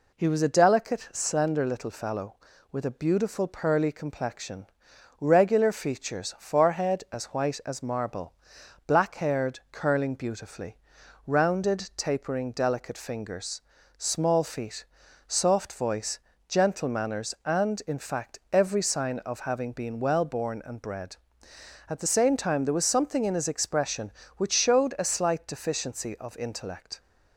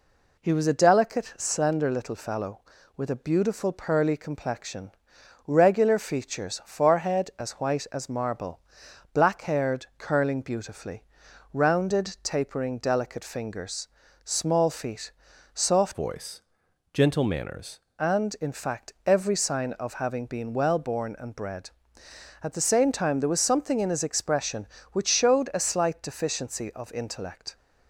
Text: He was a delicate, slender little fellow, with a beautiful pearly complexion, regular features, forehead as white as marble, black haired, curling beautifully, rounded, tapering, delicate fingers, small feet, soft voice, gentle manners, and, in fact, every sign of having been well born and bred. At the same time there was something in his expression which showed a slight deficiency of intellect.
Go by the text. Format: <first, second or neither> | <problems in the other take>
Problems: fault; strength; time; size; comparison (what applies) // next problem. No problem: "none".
first | changes voice from "voice" to "manners"; from 15.9 to 17.7 s; 1.8 s long